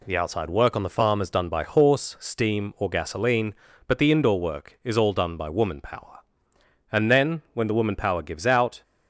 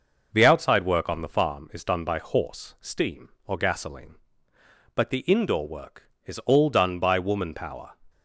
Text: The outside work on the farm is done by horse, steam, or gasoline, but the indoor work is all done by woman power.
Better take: second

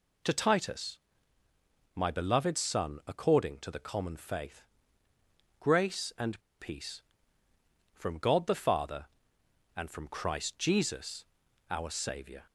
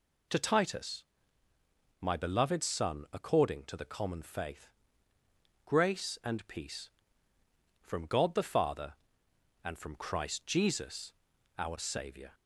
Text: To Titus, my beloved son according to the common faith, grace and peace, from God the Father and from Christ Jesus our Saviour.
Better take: second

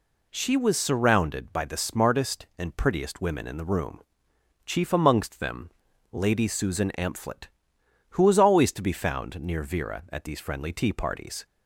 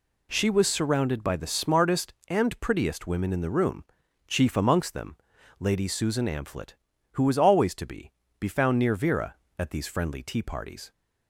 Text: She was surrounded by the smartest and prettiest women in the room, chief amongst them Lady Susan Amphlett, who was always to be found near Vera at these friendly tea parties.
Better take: first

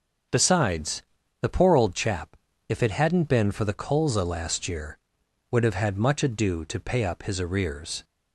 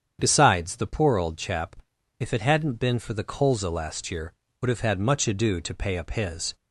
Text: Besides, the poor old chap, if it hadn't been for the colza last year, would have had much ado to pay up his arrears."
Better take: first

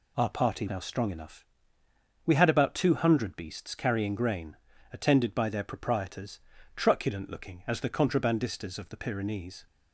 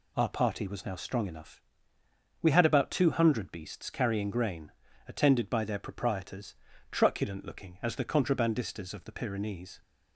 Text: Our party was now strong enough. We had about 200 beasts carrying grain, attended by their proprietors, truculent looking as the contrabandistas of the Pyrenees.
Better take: second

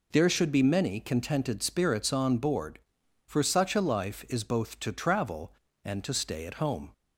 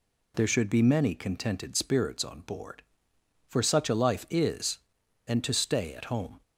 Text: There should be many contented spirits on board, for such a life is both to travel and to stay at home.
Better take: first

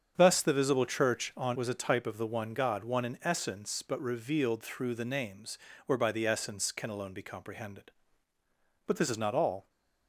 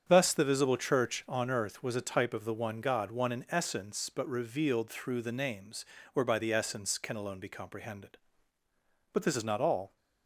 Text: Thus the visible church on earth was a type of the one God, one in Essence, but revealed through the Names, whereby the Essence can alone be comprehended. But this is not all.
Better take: second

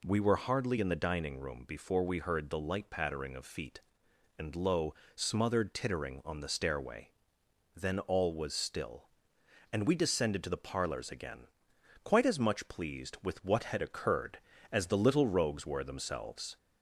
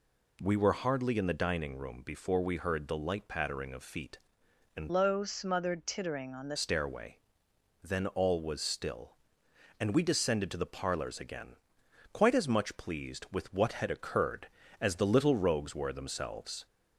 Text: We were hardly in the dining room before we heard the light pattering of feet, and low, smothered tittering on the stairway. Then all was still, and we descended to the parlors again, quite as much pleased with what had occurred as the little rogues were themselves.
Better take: first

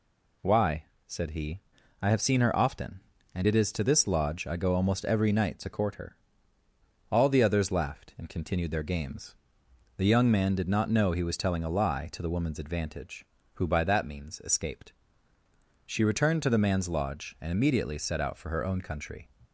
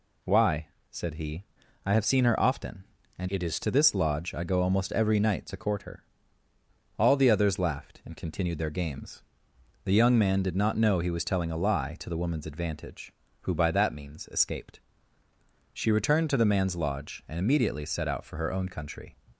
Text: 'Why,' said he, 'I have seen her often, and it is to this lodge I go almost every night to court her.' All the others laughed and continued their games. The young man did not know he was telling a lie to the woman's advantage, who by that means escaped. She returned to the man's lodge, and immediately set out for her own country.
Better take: first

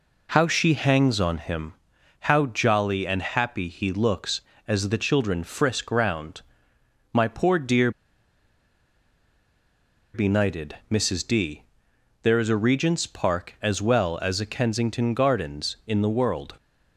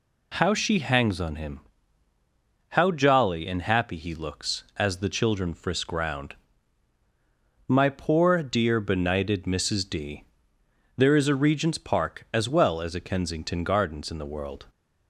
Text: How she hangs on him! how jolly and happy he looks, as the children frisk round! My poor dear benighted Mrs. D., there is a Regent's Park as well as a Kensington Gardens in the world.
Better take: second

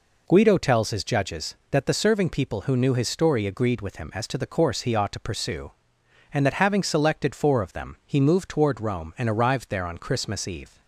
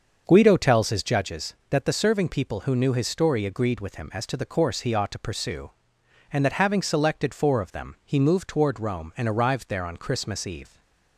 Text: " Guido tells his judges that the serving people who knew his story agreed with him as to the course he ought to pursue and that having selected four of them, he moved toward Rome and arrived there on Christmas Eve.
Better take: first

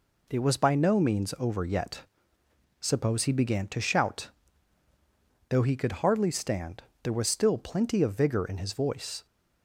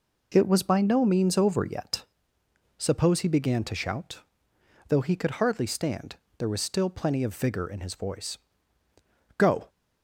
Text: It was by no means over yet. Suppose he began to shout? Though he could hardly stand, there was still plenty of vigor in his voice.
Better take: first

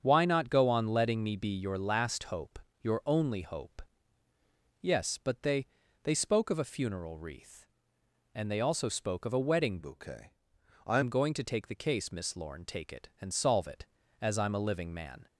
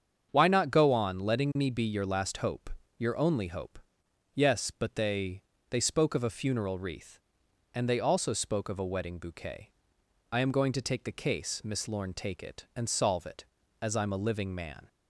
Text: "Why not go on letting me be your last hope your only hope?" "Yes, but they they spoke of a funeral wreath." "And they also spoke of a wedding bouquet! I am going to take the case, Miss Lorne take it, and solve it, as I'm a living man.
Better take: second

